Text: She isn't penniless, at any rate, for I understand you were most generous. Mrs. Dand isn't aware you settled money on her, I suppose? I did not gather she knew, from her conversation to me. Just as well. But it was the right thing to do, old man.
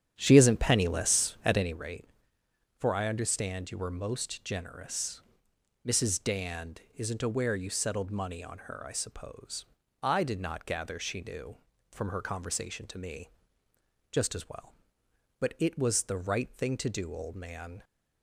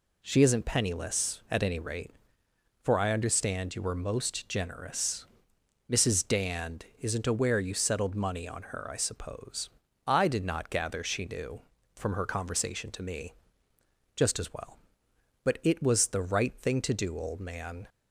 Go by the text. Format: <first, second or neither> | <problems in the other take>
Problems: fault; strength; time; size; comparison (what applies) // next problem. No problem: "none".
second | starts louder than the rest; strong; until 1.8 s; 9.5 dB